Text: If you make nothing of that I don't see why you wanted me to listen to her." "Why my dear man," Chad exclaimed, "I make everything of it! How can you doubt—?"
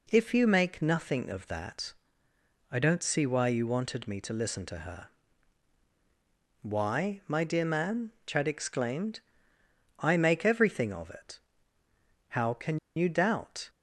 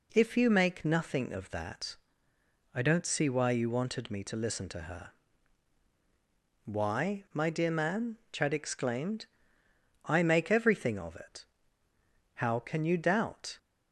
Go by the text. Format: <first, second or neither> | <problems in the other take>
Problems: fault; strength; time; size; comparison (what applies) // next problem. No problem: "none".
second | pauses between "that" and "I"; noticeable; at 1.9 s; 0.80 s long; noticeable in the second // pauses between "can" and "you"; slight; at 12.7 s; 0.18 s long